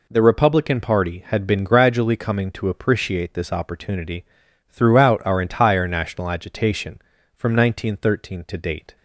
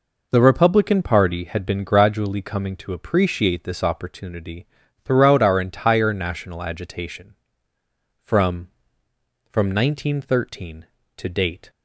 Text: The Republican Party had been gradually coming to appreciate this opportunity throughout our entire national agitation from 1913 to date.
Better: first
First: pauses between "opportunity" and "throughout"; noticeable; at 4.2 s; 0.46 s long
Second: pauses between "opportunity" and "throughout"; at 4.6 s; 0.38 s long // says "from" twice; at 9.5 s

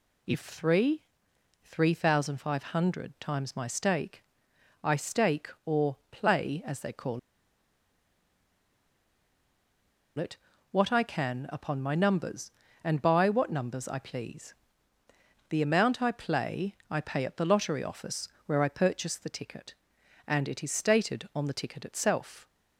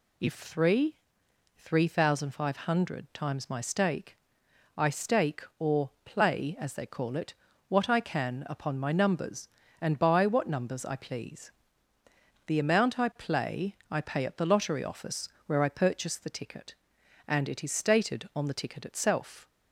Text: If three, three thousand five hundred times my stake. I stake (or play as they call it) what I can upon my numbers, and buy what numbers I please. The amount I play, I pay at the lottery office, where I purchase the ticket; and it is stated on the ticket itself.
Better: second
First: pauses between "or" and "play"; slight; at 5.9 s; 0.16 s long // pauses between "call" and "it"; strong; at 7.1 s; 2.9 s long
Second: pauses between "or" and "play"; slight; at 5.8 s; 0.16 s long

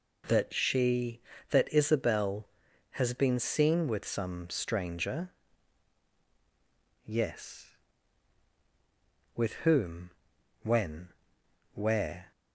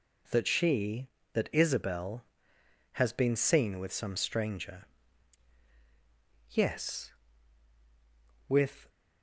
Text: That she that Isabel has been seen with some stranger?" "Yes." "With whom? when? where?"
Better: first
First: none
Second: stops before "whom when where"; at 8.8 s

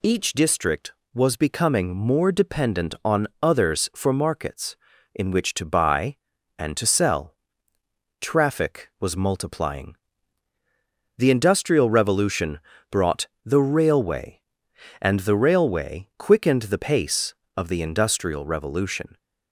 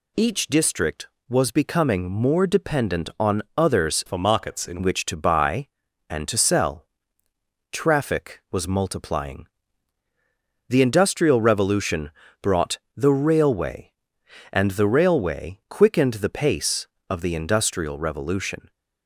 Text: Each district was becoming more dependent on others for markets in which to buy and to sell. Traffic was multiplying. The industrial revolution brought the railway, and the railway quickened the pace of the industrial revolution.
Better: first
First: pauses between "on" and "others"; slight; at 3.2 s; 0.16 s long // pauses between "revolution" and "brought"; slight; at 12.6 s; 0.30 s long // pauses between "brought" and "the"; slight; at 13.2 s; 0.18 s long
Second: pauses between "on" and "others"; slight; at 3.4 s; 0.16 s long // changes voice from "for" to "in"; from 4.0 to 4.8 s; 0.8 s long // pauses between "revolution" and "brought"; slight; at 12.1 s; 0.30 s long // pauses between "brought" and "the"; slight; at 12.7 s; 0.18 s long

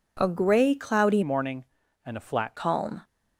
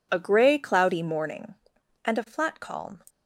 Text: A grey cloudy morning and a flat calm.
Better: second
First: changes voice from "morning" to "flat"; from 1.2 to 2.5 s; 1.3 s long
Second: none

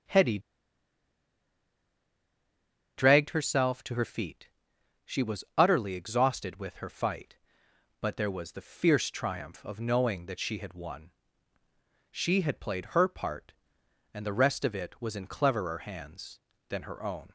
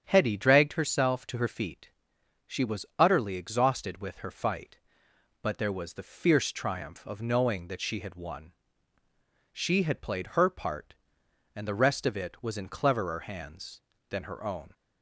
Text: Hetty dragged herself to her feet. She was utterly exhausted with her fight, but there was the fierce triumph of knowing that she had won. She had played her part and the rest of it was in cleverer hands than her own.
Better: second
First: starts louder than the rest; strong; until 3.6 s; 8 dB // pauses between "Hetty" and "dragged"; strong; at 0.3 s; 2.5 s long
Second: starts louder than the rest; strong; until 1.0 s; 8 dB

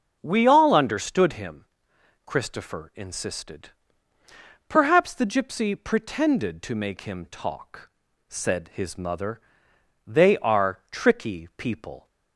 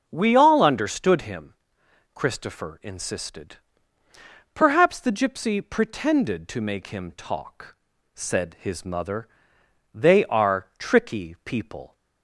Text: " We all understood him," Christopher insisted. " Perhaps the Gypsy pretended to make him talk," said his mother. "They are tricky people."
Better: neither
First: starts louder than the rest; until 1.2 s; 7 dB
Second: starts louder than the rest; until 1.1 s; 7 dB

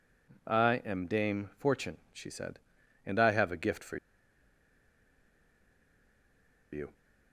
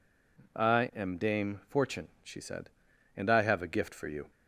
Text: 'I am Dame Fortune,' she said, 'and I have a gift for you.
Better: second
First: pauses between "for" and "you"; strong; at 3.9 s; 2.7 s long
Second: none

